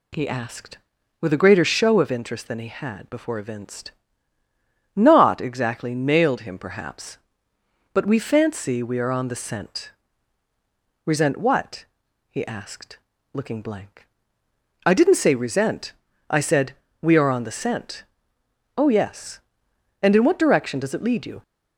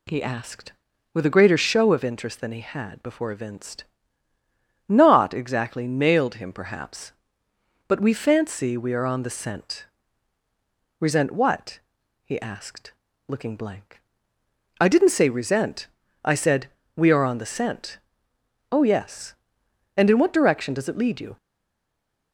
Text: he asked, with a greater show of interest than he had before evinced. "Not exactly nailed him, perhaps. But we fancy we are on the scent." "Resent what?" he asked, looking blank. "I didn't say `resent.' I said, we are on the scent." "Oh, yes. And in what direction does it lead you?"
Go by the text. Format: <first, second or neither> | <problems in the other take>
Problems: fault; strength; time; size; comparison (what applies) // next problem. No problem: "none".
first | stays silent after the last word; from 21.3 s on; 1.0 s long